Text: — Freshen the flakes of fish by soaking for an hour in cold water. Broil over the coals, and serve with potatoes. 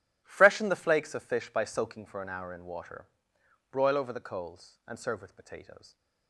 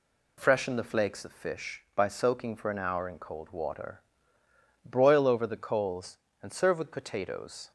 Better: second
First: skips "cold"; at 2.6 s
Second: none

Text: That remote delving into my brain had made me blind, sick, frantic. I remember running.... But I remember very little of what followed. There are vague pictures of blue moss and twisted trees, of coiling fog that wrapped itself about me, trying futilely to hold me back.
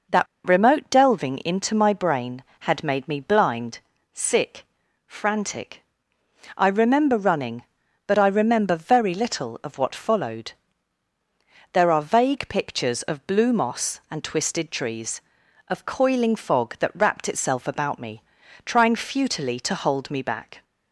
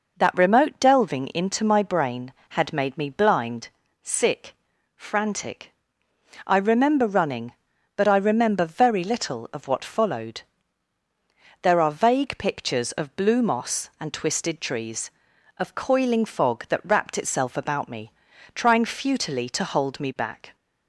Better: second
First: pauses between "That" and "remote"; slight; at 0.2 s; 0.21 s long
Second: none

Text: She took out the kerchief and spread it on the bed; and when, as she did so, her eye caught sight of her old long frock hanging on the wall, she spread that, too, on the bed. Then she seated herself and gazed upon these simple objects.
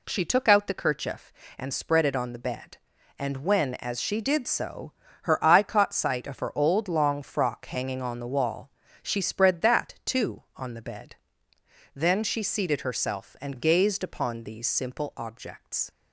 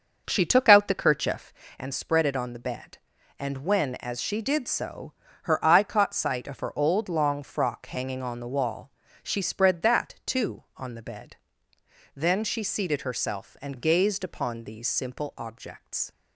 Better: first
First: none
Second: starts louder than the rest; until 1.7 s; 6.5 dB

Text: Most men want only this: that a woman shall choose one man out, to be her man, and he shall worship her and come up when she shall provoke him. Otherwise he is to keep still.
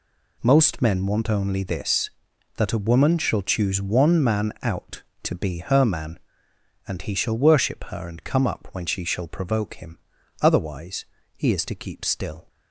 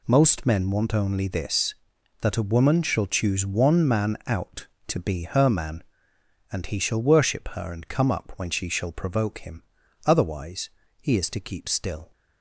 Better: neither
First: pauses between "Otherwise" and "he"; slight; at 11.0 s; 0.32 s long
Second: pauses between "Otherwise" and "he"; slight; at 10.6 s; 0.32 s long

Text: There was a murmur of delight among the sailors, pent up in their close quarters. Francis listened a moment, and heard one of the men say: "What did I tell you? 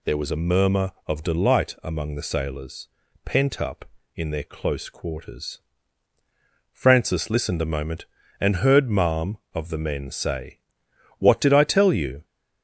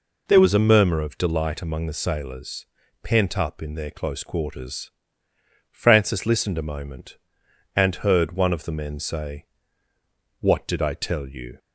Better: second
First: says "marm" for "one"; at 8.9 s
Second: none

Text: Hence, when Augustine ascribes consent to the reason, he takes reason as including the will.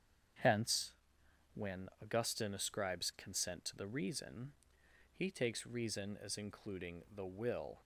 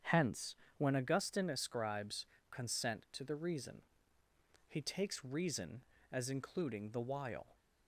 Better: first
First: starts louder than the rest; strong; until 2.1 s; 8 dB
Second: starts louder than the rest; strong; until 1.2 s; 8 dB // pauses between "ascribes" and "consent"; slight; at 2.2 s; 0.26 s long // says "while" for "will"; at 7.0 s

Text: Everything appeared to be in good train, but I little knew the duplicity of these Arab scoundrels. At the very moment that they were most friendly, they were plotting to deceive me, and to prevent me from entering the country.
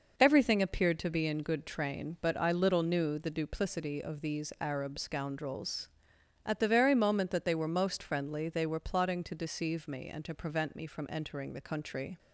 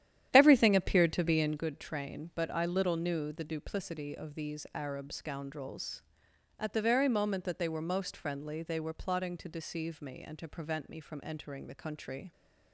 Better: first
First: none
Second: starts louder than the rest; strong; until 1.7 s; 11 dB

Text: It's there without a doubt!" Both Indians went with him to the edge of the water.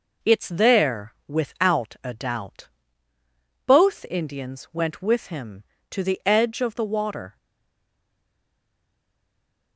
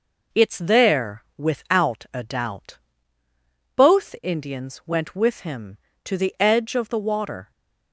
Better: second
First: stays silent after the last word; from 7.3 s on; 2.4 s long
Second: none

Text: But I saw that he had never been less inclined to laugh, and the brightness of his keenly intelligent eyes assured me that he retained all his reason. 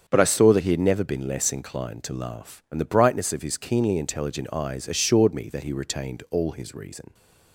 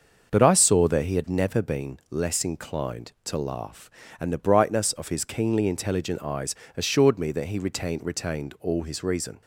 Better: first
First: starts louder than the rest; strong; until 1.0 s; 7.5 dB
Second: starts louder than the rest; until 1.3 s; 6.5 dB // pauses between "eyes" and "assured"; slight; at 6.5 s; 0.22 s long // says "retained" twice; at 8.0 s

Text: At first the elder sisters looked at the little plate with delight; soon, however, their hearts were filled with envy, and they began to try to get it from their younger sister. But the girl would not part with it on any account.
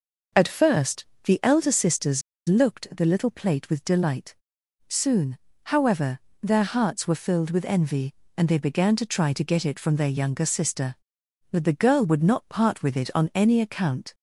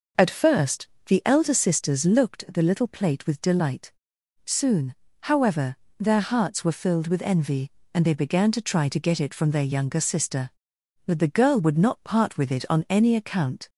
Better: second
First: pauses between "first" and "the"; slight; at 1.0 s; 0.20 s long // pauses between "sisters" and "looked"; slight; at 2.2 s; 0.26 s long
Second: pauses between "first" and "the"; slight; at 0.8 s; 0.20 s long

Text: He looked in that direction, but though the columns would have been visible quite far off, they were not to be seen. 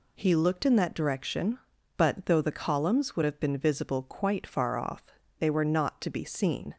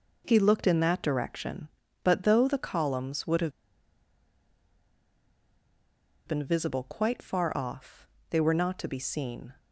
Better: first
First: none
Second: pauses between "have" and "been"; strong; at 3.5 s; 2.7 s long

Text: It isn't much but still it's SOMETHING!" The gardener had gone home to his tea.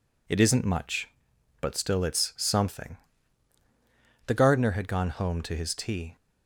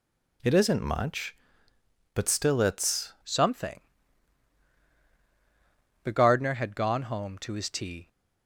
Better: first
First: none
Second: changes voice at "SOMETHING"; from 3.2 s on; 4.8 s long

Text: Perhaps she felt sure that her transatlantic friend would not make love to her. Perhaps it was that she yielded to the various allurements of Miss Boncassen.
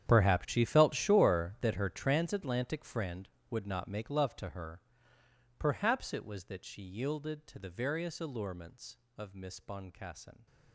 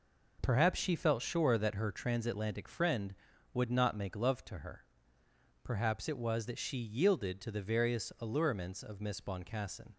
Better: second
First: gets quieter; strong; throughout; 18 dB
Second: none

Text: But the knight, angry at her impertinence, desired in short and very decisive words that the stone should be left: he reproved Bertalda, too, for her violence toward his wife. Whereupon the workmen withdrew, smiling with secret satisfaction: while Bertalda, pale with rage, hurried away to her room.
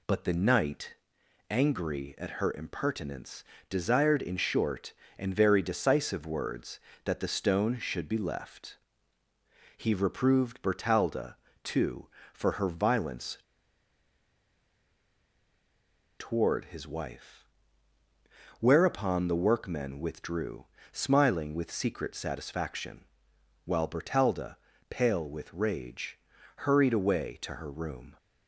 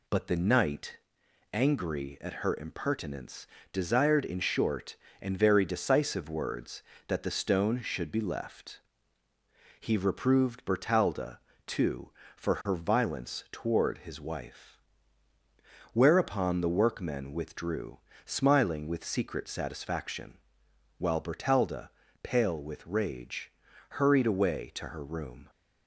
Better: second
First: pauses between "violence" and "toward"; strong; at 13.3 s; 2.8 s long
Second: none

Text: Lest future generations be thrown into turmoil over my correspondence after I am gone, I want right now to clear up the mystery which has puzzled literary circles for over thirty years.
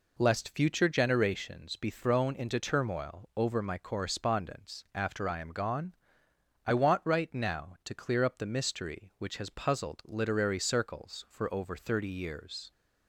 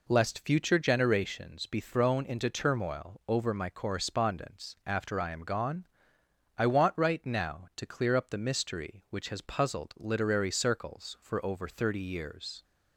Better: neither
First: none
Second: none

